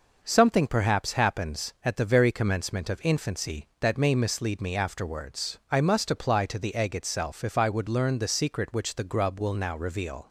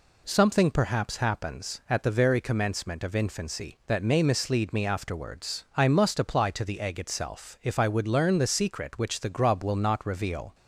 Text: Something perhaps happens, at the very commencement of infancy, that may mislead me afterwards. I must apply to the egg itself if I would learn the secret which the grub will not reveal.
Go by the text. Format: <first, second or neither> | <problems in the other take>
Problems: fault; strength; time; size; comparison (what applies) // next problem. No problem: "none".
second | says "now" for "not"; at 9.5 s